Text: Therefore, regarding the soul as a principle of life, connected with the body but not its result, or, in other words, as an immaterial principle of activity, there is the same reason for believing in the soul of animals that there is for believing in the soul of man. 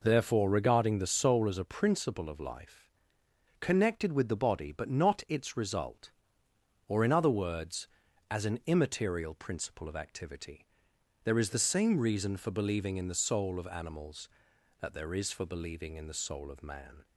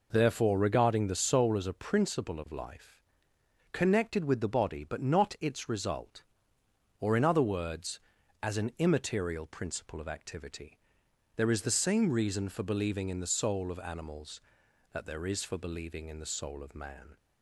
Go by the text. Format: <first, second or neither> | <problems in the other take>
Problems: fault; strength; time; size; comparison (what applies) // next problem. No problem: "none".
neither | none